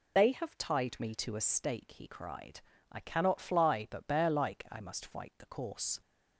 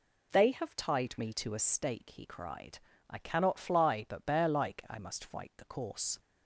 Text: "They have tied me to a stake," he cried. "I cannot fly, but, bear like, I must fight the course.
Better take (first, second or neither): second